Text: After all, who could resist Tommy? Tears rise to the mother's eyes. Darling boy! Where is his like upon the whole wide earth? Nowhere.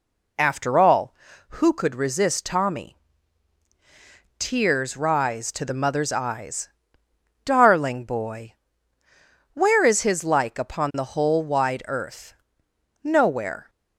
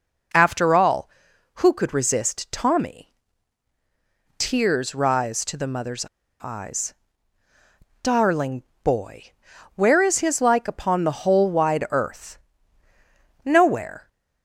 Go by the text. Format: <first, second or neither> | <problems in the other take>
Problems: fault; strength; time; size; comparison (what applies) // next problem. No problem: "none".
first | pauses between "mother's" and "eyes"; slight; at 6.0 s; 0.35 s long // pauses between "Darling" and "boy"; slight; at 8.6 s; 0.20 s long